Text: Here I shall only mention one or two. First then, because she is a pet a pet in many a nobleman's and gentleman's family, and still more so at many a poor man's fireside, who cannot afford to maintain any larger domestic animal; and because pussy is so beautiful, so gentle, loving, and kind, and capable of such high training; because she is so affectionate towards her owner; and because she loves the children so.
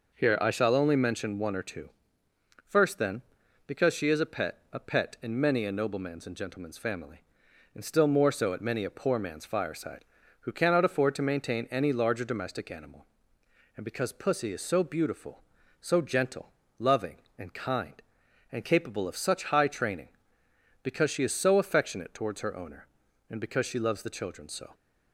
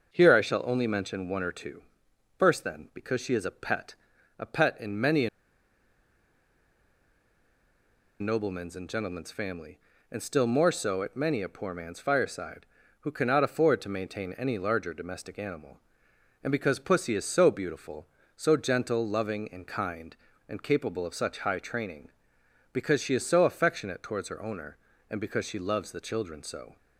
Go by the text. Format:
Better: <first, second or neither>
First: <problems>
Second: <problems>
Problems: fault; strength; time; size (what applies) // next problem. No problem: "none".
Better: first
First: none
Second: starts louder than the rest; until 1.1 s; 6.5 dB // pauses between "pet" and "a"; at 3.9 s; 0.44 s long // pauses between "a" and "nobleman's"; strong; at 5.2 s; 2.9 s long